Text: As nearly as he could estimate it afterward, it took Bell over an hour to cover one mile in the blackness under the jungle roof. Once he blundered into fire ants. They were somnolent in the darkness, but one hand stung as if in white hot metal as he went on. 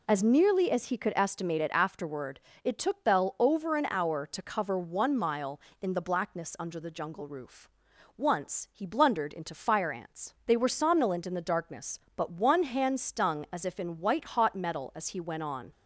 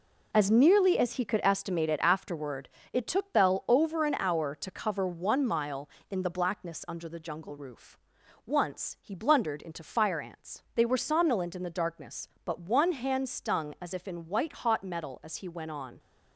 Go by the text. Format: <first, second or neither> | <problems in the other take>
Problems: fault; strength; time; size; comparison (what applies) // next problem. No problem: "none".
first | gets quieter; strong; throughout; 7.5 dB